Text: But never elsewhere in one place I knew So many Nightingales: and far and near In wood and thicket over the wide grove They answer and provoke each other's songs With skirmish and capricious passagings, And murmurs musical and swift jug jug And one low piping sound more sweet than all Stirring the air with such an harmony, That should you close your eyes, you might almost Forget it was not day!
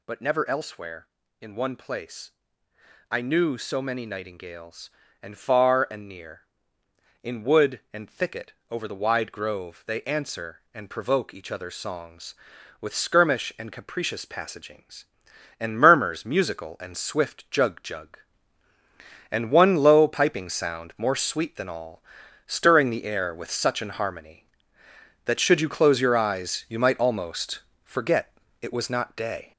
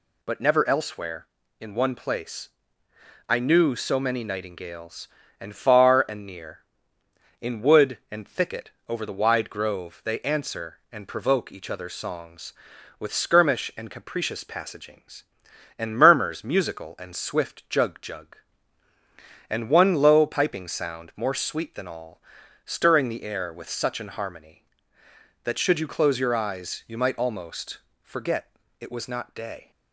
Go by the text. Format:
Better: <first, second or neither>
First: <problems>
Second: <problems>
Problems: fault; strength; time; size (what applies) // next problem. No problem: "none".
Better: second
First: gets louder; noticeable; throughout; 5.5 dB // pauses between "place" and "I"; noticeable; at 2.3 s; 0.78 s long // pauses between "thicket" and "over"; slight; at 8.5 s; 0.16 s long // pauses between "all" and "Stirring"; noticeable; at 22.0 s; 0.46 s long // pauses between "almost" and "Forget"; slight; at 27.5 s; 0.24 s long // pauses between "Forget" and "it"; slight; at 28.3 s; 0.30 s long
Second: pauses between "place" and "I"; noticeable; at 2.5 s; 0.78 s long // pauses between "thicket" and "over"; slight; at 8.7 s; 0.16 s long // pauses between "all" and "Stirring"; noticeable; at 22.2 s; 0.46 s long // pauses between "almost" and "Forget"; slight; at 27.7 s; 0.24 s long // pauses between "Forget" and "it"; slight; at 28.5 s; 0.30 s long